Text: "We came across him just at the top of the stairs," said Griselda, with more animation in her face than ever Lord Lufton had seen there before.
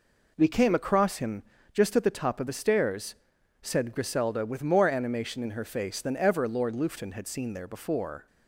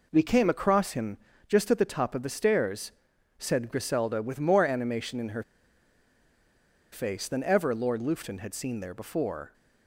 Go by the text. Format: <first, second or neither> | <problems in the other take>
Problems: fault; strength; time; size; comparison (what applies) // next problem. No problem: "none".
first | pauses between "him" and "just"; slight; at 1.1 s; 0.28 s long; slight in the first // pauses between "her" and "face"; strong; at 5.4 s; 1.4 s long